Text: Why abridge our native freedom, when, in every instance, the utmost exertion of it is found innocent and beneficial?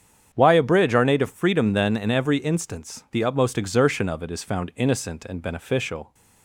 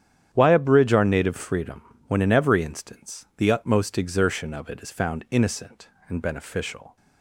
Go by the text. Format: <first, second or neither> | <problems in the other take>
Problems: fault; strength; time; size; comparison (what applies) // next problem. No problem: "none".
second | starts louder than the rest; strong; until 1.3 s; 8.5 dB; strong in the second // says "then" for "when"; at 1.7 s